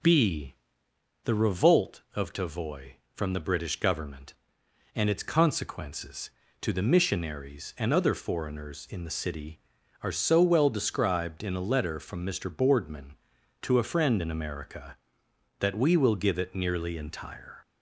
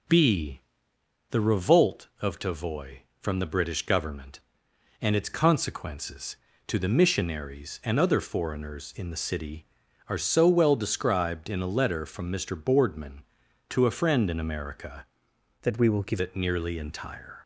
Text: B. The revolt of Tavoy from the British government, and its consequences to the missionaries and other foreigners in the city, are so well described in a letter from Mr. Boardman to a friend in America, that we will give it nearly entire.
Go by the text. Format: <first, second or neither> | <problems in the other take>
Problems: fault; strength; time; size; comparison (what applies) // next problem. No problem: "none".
first | changes voice from "that" to "give"; from 15.6 to 16.2 s; 0.6 s long